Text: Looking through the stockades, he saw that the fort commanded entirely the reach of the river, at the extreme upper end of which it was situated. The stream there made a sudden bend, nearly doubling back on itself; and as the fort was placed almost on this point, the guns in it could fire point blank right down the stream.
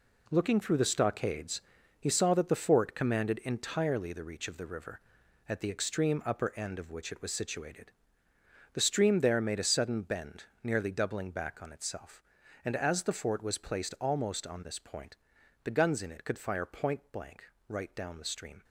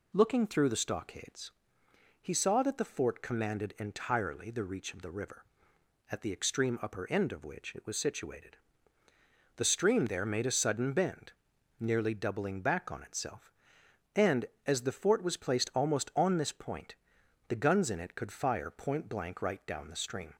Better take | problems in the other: second | gets quieter; strong; throughout; 9 dB // pauses between "blank" and "right"; slight; at 17.4 s; 0.24 s long

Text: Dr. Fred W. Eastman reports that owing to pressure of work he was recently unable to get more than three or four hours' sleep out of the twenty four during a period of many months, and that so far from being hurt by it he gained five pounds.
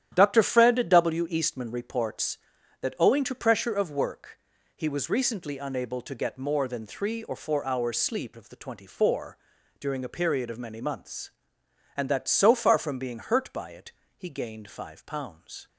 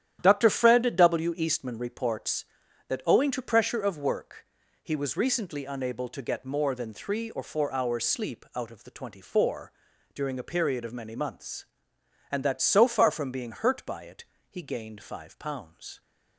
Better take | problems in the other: second | starts louder than the rest; strong; until 1.1 s; 10.5 dB; strong in the second // pauses between "work" and "he"; at 4.3 s; 0.38 s long; also in the second // skips "out"; at 8.3 s // pauses between "four" and "during"; at 9.3 s; 0.42 s long; also in the second // pauses between "it" and "he"; slight; at 13.9 s; 0.26 s long; slight in the second

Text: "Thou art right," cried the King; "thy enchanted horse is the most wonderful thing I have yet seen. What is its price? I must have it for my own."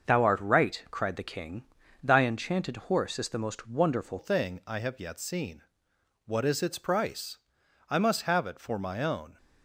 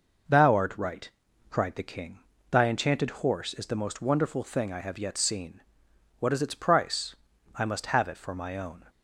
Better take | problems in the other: second | starts louder than the rest; until 1.1 s; 6.5 dB // changes voice at "thing"; from 4.1 s on; 5.2 s long

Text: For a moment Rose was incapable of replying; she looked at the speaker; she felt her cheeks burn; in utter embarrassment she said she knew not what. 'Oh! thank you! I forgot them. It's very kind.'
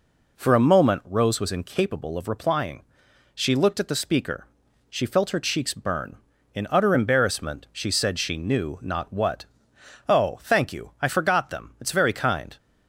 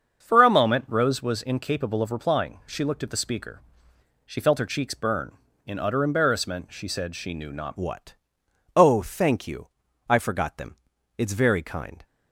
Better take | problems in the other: first | starts louder than the rest; until 1.2 s; 6.5 dB // changes voice at "what"; from 7.7 s on; 4.3 s long

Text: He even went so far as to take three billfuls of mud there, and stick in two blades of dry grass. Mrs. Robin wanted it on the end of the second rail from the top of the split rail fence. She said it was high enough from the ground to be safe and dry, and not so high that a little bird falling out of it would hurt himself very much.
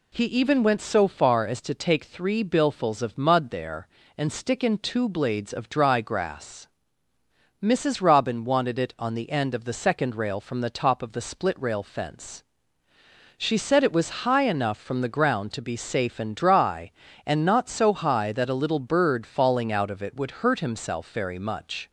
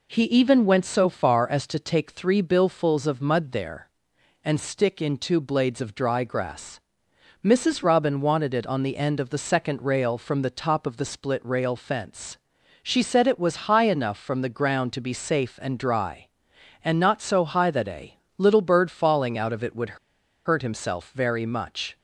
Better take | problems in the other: first | pauses between "a" and "little"; slight; at 18.1 s; 0.20 s long // pauses between "would" and "hurt"; noticeable; at 19.9 s; 0.49 s long

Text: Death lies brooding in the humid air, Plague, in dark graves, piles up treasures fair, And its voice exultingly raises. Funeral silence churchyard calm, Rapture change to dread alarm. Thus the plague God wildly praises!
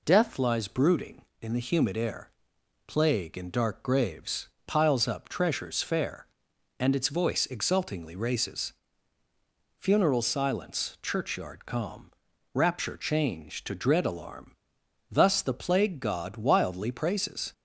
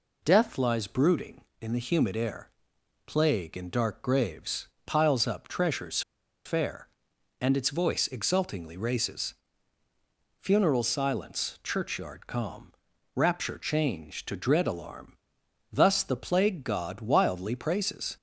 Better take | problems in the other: first | pauses between "treasures" and "fair"; at 6.0 s; 0.44 s long

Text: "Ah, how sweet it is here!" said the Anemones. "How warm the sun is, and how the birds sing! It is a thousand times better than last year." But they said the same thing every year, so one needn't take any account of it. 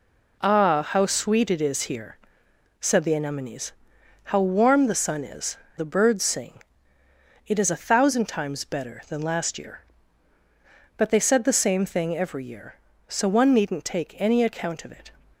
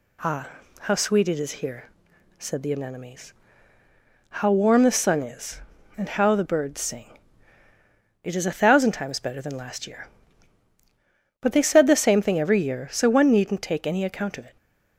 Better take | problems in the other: second | skips "and how"; at 5.6 s

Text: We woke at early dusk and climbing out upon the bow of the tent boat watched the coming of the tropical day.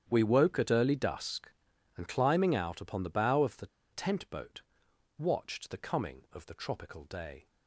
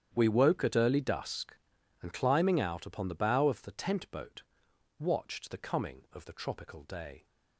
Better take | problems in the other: second | starts louder than the rest; strong; until 1.1 s; 9 dB; strong in the second // pauses between "the" and "tent"; slight; at 3.6 s; 0.27 s long // pauses between "boat" and "watched"; noticeable; at 4.6 s; 0.56 s long; noticeable in the second

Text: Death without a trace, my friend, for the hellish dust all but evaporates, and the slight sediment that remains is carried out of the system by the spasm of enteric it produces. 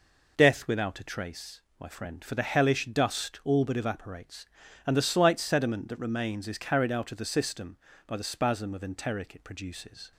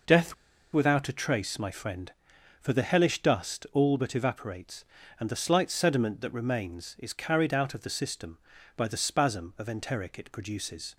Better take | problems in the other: first | pauses between "Death" and "without"; at 0.3 s; 0.39 s long

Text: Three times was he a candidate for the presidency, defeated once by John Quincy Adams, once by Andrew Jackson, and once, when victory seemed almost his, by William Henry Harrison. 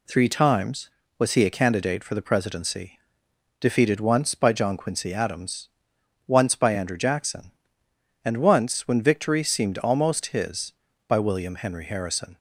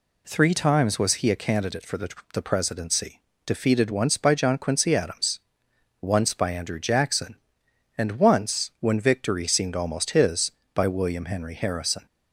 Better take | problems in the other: first | says "the" twice; at 2.3 s

